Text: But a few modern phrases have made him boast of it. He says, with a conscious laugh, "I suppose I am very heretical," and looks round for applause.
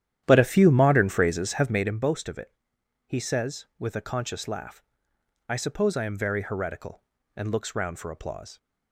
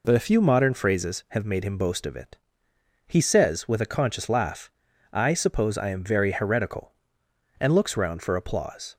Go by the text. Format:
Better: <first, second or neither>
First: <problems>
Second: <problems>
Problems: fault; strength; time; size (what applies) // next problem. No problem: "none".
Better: second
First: starts louder than the rest; strong; until 1.9 s; 11 dB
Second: none